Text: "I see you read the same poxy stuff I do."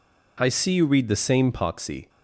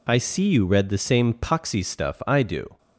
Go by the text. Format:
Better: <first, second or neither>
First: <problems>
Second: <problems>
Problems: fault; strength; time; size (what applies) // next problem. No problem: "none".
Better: second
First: stops before "stuff I do"; at 2.0 s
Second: none